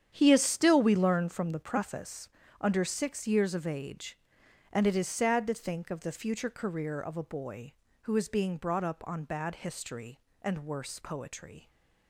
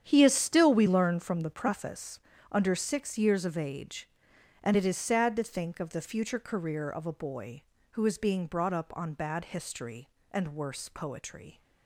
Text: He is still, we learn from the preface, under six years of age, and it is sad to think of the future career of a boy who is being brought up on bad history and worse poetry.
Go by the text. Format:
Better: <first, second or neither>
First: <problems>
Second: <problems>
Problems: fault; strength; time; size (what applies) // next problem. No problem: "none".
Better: neither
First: starts louder than the rest; strong; until 1.1 s; 9 dB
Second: starts louder than the rest; strong; until 1.0 s; 9 dB